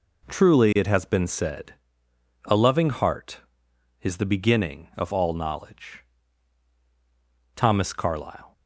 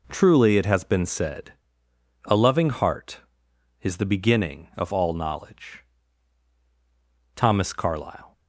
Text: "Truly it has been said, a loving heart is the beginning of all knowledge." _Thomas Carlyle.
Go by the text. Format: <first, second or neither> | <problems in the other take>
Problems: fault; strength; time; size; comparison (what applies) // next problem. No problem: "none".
neither | none